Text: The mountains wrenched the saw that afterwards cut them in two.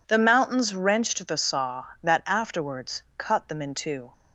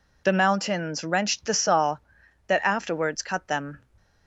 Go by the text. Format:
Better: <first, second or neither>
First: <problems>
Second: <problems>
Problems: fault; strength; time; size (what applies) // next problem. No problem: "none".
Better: first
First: none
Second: stops before "in two"; at 3.9 s